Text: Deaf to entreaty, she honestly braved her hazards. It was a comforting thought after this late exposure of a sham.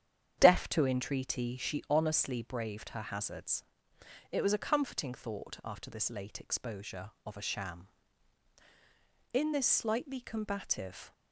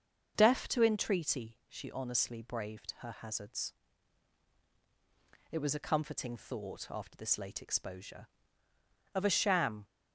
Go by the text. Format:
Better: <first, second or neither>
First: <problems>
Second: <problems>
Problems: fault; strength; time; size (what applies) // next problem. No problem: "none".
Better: second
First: starts louder than the rest; strong; until 1.4 s; 9 dB // goes on to say "In this slightly combative"; strong; from 9.3 s on; 1.7 s long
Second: starts louder than the rest; until 1.3 s; 6.5 dB